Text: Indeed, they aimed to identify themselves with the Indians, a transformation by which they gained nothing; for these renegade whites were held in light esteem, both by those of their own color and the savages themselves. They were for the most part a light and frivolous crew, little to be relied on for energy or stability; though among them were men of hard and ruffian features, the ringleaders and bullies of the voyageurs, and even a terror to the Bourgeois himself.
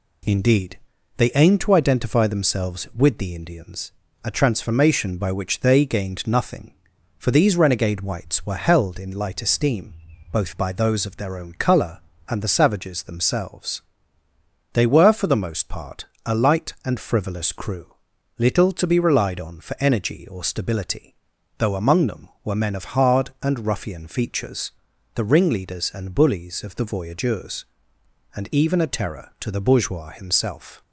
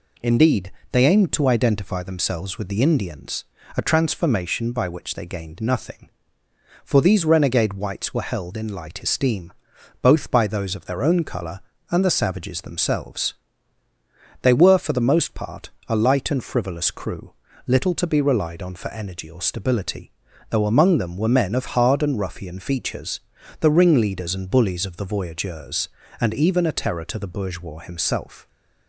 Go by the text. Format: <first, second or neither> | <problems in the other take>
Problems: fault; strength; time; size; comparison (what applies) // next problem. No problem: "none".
neither | pauses between "part" and "a"; slight; the same in both